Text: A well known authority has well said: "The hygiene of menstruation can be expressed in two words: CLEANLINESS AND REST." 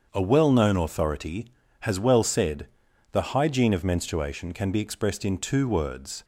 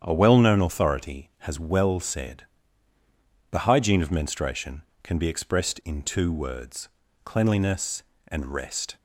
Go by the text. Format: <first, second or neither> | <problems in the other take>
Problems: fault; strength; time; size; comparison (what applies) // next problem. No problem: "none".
second | starts louder than the rest; strong; until 1.1 s; 7 dB; strong in the second // stops before "CLEANLINESS AND REST"; at 6.2 s